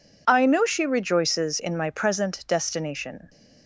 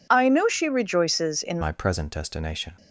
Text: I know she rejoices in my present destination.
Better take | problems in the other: first | changes voice at "my"; from 1.6 s on; 1.1 s long

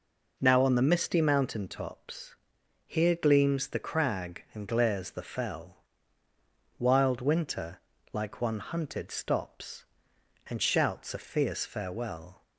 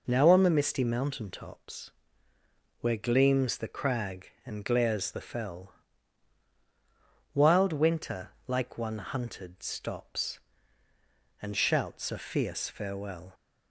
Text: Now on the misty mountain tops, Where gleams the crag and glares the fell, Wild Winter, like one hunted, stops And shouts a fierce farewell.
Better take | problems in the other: second | says "Here" for "Where"; at 2.8 s

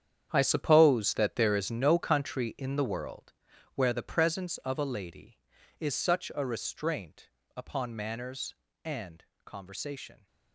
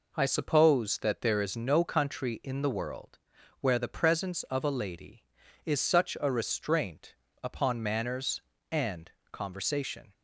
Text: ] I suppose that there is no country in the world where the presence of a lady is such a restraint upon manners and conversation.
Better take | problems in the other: second | gets quieter; strong; throughout; 13 dB // pauses between "world" and "where"; at 3.3 s; 0.44 s long; also in the second // pauses between "restraint" and "upon"; slight; at 7.2 s; 0.26 s long; slight in the second // pauses between "and" and "conversation"; slight; at 9.2 s; 0.22 s long; slight in the second

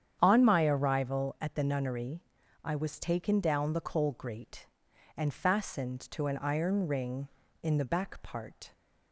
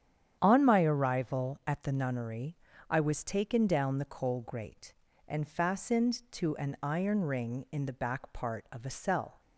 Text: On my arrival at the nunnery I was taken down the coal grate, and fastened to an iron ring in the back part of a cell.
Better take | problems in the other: second | starts louder than the rest; strong; until 1.2 s; 9 dB; strong in the second // pauses between "nunnery" and "I"; at 2.2 s; 0.40 s long; slight in the second // stops before "of a cell"; at 8.7 s

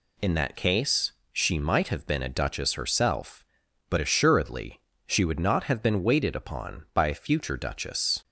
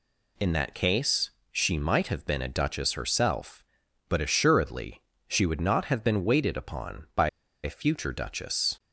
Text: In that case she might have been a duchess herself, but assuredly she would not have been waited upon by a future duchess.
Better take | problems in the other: first | pauses between "case" and "she"; slight; at 1.3 s; 0.20 s long; slight in the first // pauses between "assuredly" and "she"; slight; at 5.0 s; 0.26 s long; slight in the first // pauses between "by" and "a"; slight; at 7.2 s; 0.35 s long

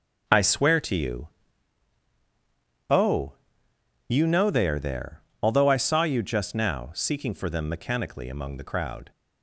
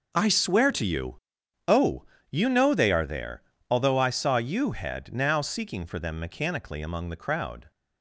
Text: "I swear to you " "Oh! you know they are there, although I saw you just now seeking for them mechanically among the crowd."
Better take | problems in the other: first | says "head" for "just"; at 4.7 s

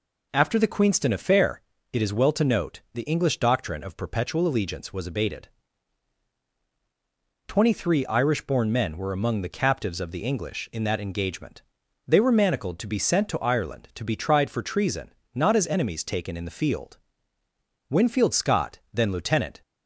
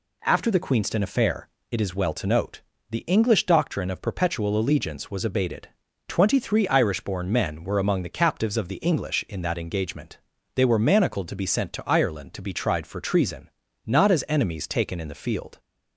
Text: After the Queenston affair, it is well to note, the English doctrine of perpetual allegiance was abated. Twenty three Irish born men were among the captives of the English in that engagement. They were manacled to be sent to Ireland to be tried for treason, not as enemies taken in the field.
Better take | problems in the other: second | goes on to say "Winfield Scott then lieutenant"; strong; from 17.8 s on; 1.7 s long

